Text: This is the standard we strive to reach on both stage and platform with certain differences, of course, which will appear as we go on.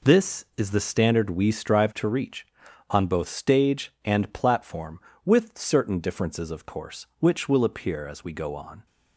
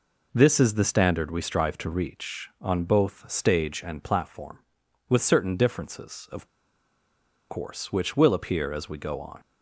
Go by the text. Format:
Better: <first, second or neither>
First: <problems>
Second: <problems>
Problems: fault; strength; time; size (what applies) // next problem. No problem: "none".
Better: first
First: none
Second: pauses between "of" and "course"; at 6.4 s; 1.0 s long